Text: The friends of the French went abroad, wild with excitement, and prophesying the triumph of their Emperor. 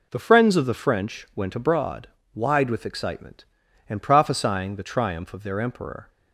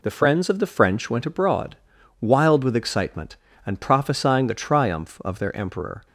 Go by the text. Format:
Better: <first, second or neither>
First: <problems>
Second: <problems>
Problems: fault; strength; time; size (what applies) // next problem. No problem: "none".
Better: second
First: says "wide" for "wild"; at 2.3 s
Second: none